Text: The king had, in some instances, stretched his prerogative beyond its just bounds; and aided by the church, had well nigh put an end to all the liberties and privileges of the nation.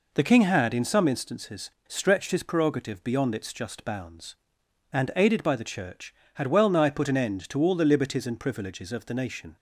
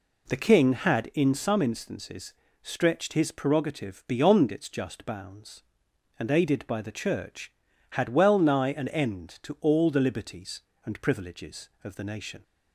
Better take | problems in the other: first | skips "put"; at 8.7 s

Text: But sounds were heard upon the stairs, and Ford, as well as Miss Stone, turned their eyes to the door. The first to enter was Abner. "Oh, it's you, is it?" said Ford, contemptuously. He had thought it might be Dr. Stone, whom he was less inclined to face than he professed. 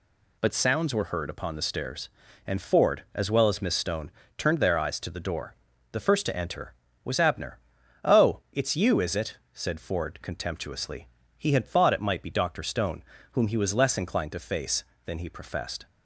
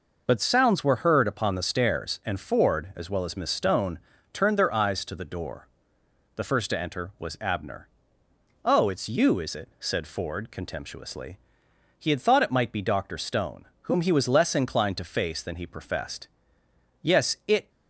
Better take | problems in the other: first | goes on to say "Yes it"; noticeable; from 17.0 s on; 0.66 s long

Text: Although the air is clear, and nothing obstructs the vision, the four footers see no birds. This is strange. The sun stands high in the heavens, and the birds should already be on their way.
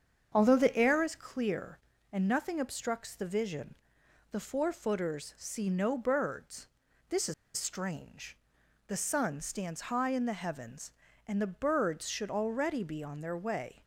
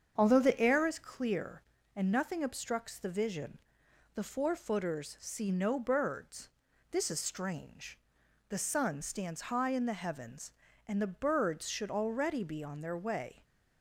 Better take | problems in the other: second | starts louder than the rest; strong; until 1.3 s; 7.5 dB; strong in the second // pauses between "is" and "strange"; slight; at 7.3 s; 0.23 s long

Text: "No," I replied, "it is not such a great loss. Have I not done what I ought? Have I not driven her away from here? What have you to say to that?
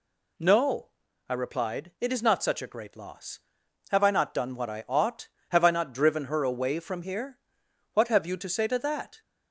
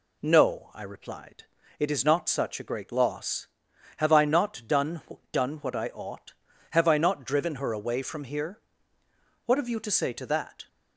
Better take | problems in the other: first | says "done" twice; at 5.3 s

